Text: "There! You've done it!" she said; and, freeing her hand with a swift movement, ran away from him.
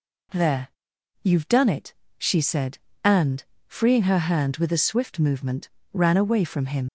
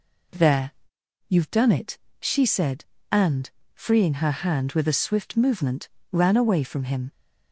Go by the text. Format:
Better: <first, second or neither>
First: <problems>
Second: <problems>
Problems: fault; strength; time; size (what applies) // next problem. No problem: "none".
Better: second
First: leaves "him" unfinished; at 6.8 s; 65 ms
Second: none